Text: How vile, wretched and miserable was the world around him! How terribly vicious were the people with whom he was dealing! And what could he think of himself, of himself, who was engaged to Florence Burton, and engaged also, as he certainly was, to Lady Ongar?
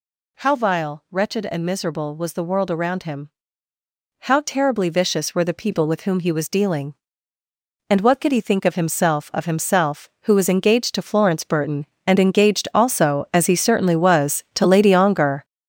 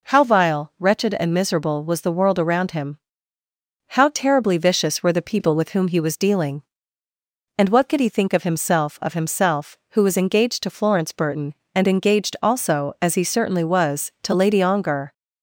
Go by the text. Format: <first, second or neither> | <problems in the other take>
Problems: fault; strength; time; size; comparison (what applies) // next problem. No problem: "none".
second | gets louder; strong; throughout; 9 dB